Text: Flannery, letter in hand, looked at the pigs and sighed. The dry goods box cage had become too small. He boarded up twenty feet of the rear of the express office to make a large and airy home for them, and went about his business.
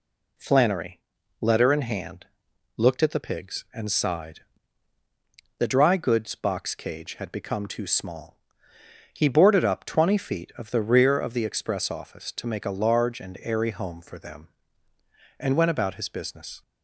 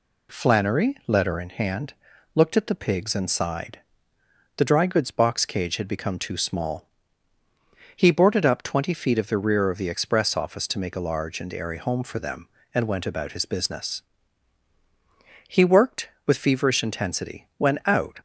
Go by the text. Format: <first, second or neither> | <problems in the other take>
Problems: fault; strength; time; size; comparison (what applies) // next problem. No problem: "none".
first | goes on to say "He worked with feverish intensity when out"; strong; from 15.4 s on; 2.7 s long